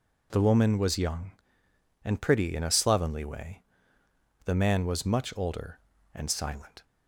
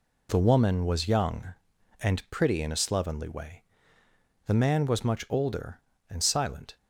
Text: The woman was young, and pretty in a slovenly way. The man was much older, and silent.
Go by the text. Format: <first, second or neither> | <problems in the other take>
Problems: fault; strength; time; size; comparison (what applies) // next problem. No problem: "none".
neither | none